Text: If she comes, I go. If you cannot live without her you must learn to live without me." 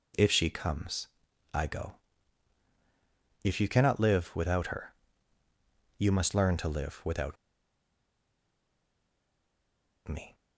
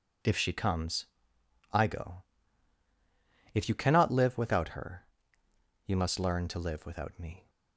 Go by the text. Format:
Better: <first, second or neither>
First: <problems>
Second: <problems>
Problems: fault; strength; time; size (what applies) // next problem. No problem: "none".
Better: second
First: pauses between "her" and "you"; at 4.9 s; 1.0 s long // pauses between "without" and "me"; strong; at 7.3 s; 2.7 s long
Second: pauses between "her" and "you"; noticeable; at 5.0 s; 0.78 s long